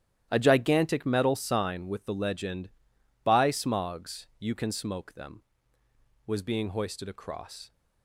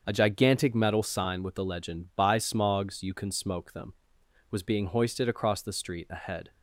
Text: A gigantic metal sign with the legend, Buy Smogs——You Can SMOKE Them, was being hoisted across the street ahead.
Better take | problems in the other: second | starts louder than the rest; strong; until 1.3 s; 12 dB; also in the second // stops before "the street ahead"; at 7.7 s

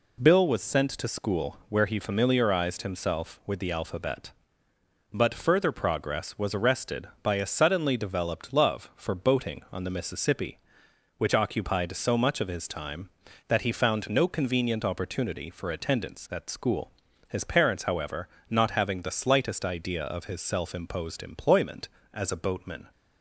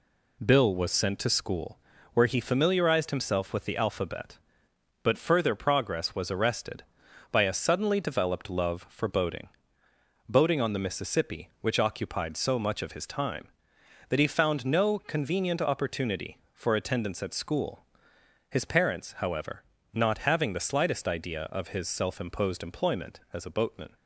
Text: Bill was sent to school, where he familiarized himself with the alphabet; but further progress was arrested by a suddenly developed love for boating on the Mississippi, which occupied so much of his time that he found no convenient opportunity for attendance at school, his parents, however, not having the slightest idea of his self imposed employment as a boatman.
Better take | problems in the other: first | says "boating" twice; at 10.2 s

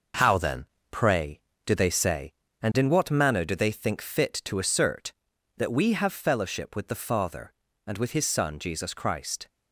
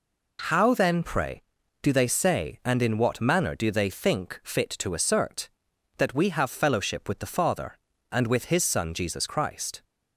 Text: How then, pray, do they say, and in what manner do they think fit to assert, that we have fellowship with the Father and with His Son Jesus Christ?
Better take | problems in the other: second | gets quieter; throughout; 7 dB

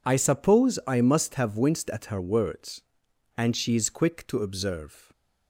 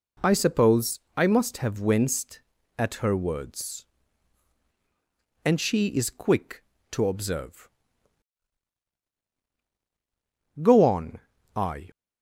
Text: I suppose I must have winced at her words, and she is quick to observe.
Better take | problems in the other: first | pauses between "suppose" and "I"; slight; at 0.9 s; 0.18 s long // goes on to say "Go on I"; noticeable; from 10.6 s on; 1.3 s long

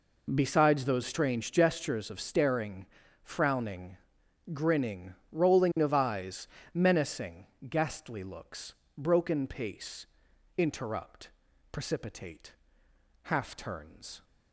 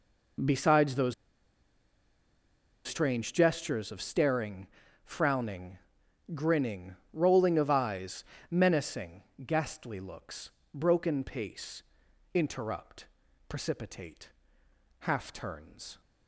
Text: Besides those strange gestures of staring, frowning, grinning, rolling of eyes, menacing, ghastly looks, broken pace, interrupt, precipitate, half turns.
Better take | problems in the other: first | pauses between "those" and "strange"; strong; at 1.1 s; 1.7 s long

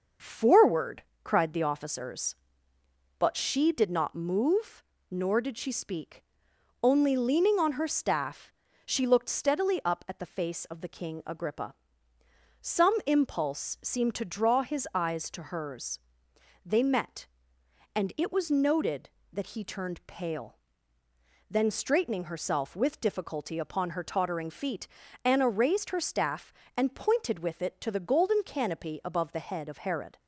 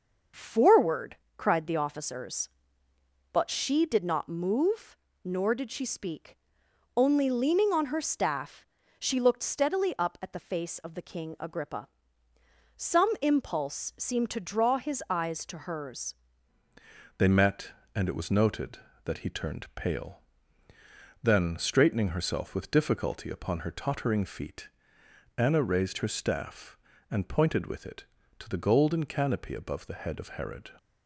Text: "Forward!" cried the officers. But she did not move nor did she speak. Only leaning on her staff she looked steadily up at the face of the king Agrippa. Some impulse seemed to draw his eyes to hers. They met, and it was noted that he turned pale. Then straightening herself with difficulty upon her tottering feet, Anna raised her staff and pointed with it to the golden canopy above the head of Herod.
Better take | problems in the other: first | starts louder than the rest; noticeable; until 1.5 s; 6 dB; noticeable in the first // pauses between "move" and "nor"; slight; at 4.9 s; 0.28 s long; slight in the first // pauses between "staff" and "she"; slight; at 8.6 s; 0.34 s long; slight in the first // changes voice at "They"; from 17.1 s on; 13.6 s long

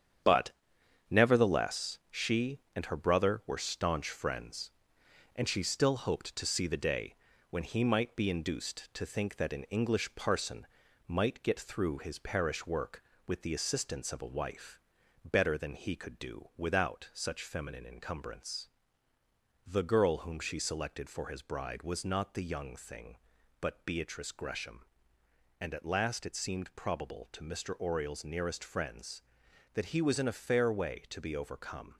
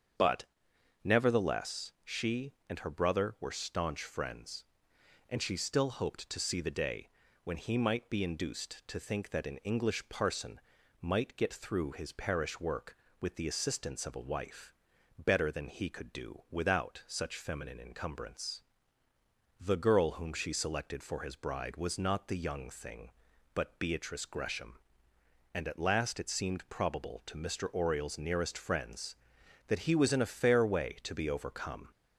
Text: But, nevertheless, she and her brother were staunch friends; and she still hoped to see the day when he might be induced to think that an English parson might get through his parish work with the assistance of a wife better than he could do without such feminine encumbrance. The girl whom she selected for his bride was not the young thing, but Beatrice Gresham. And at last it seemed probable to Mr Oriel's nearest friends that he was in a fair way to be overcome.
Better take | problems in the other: second | gets quieter; noticeable; throughout; 6 dB // starts louder than the rest; strong; until 1.8 s; 8.5 dB; strong in the second // pauses between "day" and "when"; slight; at 7.1 s; 0.36 s long; slight in the second // pauses between "parson" and "might"; at 10.6 s; 0.42 s long; also in the second // pauses between "wife" and "better"; noticeable; at 14.7 s; 0.46 s long; noticeable in the second

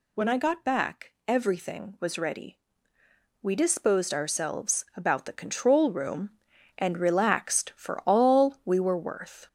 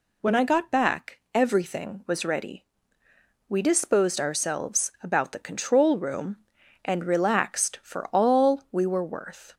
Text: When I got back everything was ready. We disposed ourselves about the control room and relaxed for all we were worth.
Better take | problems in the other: second | gets louder; noticeable; throughout; 4 dB

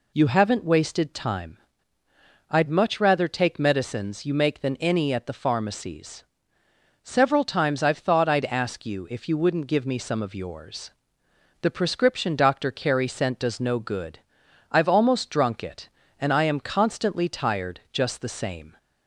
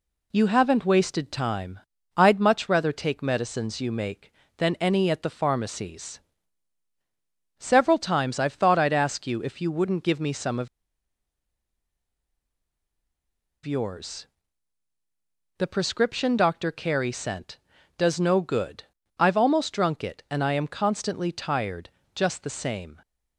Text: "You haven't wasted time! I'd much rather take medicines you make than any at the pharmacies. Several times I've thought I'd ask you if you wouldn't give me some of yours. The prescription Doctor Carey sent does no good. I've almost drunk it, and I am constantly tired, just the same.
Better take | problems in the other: first | pauses between "of" and "yours"; strong; at 10.6 s; 2.9 s long

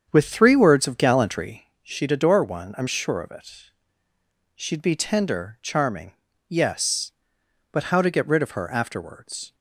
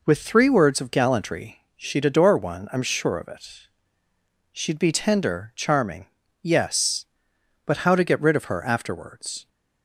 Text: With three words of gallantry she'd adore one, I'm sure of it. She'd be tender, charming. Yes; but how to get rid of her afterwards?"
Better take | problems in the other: second | starts louder than the rest; strong; until 1.5 s; 7.5 dB // pauses between "gallantry" and "she'd"; slight; at 1.6 s; 0.18 s long; slight in the second

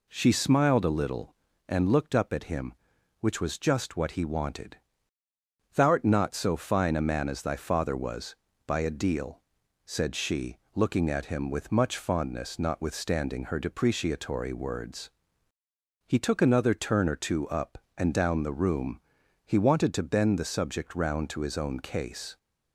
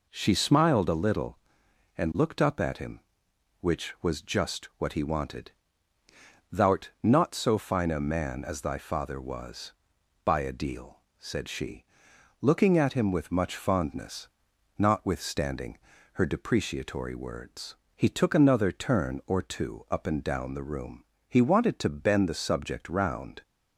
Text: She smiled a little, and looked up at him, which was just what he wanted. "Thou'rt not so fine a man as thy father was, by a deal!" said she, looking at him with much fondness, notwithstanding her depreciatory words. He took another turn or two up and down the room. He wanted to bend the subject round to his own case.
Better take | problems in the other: first | pauses between "notwithstanding" and "her"; slight; at 15.7 s; 0.36 s long // stops before "to his own case"; at 23.4 s

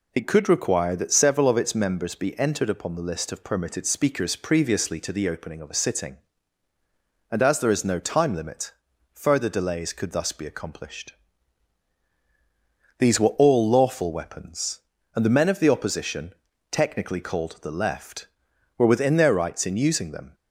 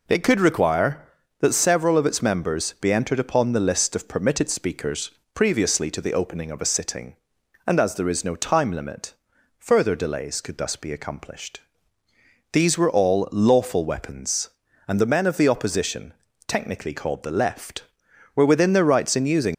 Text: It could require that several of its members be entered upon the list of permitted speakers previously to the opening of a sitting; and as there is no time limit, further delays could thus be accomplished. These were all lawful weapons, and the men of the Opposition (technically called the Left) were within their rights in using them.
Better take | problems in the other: first | pauses between "speakers" and "previously"; slight; at 5.0 s; 0.24 s long // stops before "them"; at 19.5 s

